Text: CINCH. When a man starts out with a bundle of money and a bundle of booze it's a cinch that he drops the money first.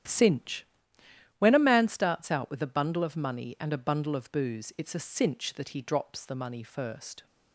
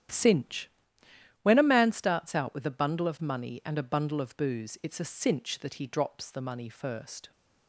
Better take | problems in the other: neither | starts louder than the rest; strong; the same in both

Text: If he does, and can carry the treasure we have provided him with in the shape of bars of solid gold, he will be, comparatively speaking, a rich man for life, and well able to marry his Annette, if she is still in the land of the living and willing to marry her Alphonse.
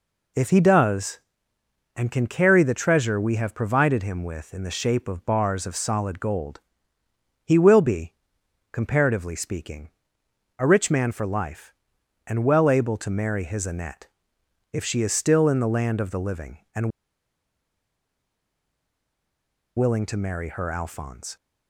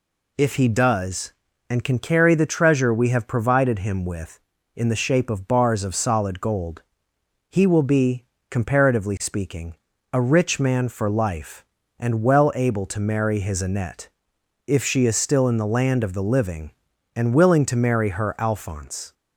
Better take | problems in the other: second | pauses between "and" and "willing"; strong; at 16.8 s; 2.8 s long

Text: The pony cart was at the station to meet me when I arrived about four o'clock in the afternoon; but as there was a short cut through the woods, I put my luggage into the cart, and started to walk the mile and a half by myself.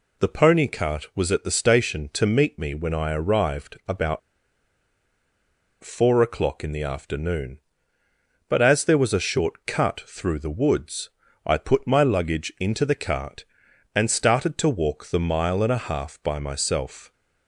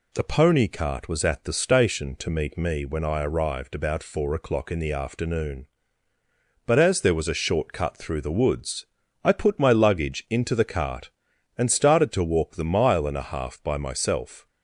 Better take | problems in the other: second | pauses between "about" and "four"; strong; at 4.1 s; 1.6 s long

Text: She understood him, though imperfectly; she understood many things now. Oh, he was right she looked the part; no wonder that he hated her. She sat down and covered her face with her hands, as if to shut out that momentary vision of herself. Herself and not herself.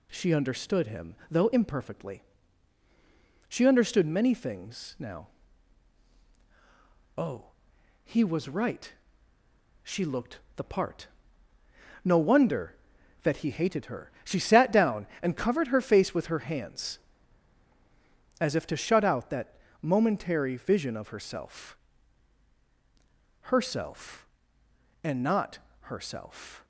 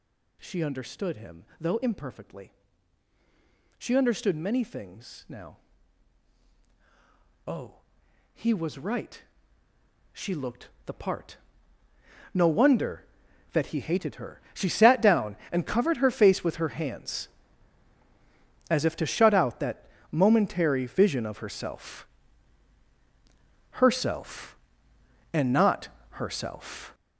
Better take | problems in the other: first | gets louder; strong; throughout; 9 dB // pauses between "right" and "she"; noticeable; at 9.2 s; 0.90 s long; noticeable in the first // pauses between "looked" and "the"; slight; at 10.6 s; 0.16 s long; slight in the first // pauses between "that" and "momentary"; slight; at 19.8 s; 0.26 s long; slight in the first // pauses between "not" and "herself"; slight; at 25.8 s; 0.24 s long; slight in the first

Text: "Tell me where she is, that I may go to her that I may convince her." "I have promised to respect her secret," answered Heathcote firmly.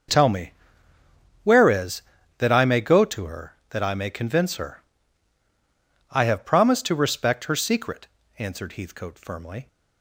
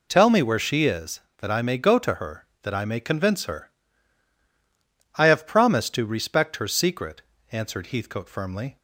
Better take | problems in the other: second | starts louder than the rest; until 2.0 s; 6 dB // pauses between "me" and "where"; noticeable; at 0.5 s; 0.90 s long // skips "she"; at 1.6 s

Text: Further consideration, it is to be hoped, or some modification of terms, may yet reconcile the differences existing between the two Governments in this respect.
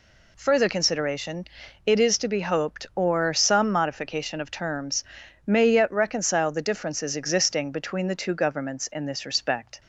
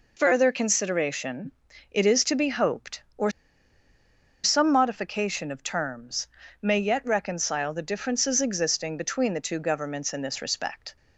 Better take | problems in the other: first | pauses between "or" and "some"; at 3.2 s; 1.1 s long

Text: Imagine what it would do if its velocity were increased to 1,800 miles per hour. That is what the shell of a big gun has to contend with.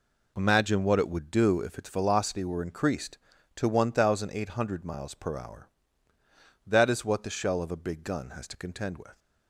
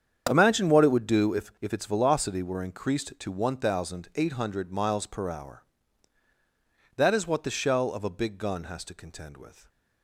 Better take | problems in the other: first | starts louder than the rest; strong; until 1.3 s; 8 dB // says "if" twice; at 1.6 s

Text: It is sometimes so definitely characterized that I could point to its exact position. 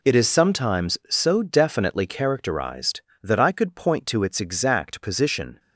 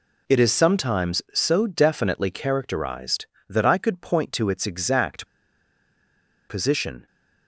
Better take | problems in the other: first | pauses between "exact" and "position"; at 5.2 s; 1.2 s long

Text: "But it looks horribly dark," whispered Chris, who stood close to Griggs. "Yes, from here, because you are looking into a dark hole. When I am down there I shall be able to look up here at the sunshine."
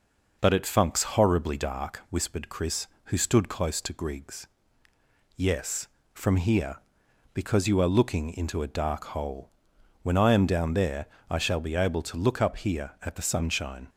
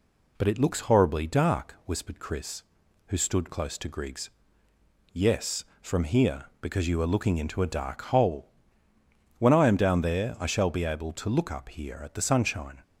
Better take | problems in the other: second | says "funks" for "looks"; at 0.6 s // pauses between "there" and "I"; slight; at 11.0 s; 0.22 s long

